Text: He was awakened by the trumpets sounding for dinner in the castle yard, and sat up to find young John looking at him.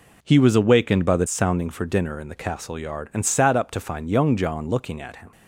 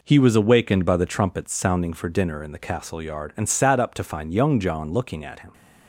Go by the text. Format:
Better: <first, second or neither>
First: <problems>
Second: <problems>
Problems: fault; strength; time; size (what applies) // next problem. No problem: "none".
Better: second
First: skips "trumpets"; at 1.2 s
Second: none